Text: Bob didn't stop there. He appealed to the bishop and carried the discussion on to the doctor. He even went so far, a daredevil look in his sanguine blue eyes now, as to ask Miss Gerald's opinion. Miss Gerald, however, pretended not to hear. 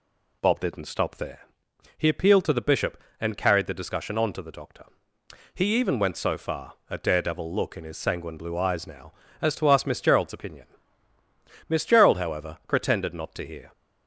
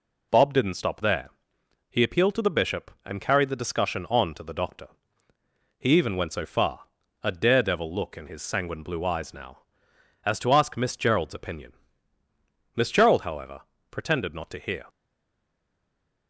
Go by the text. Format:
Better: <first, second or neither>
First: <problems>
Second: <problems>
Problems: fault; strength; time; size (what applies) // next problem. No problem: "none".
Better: first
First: none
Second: stays silent after the last word; noticeable; from 14.8 s on; 1.4 s long